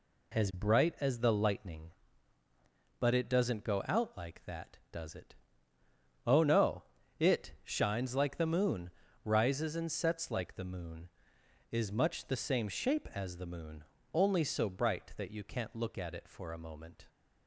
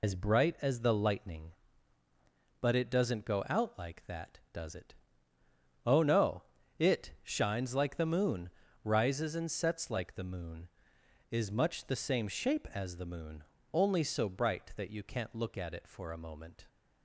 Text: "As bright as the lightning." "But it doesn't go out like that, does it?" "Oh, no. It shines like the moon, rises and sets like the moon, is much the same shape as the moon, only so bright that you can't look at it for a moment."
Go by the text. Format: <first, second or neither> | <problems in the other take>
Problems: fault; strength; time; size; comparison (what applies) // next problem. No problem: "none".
first | loses the start of "As"; at 0.0 s; 85 ms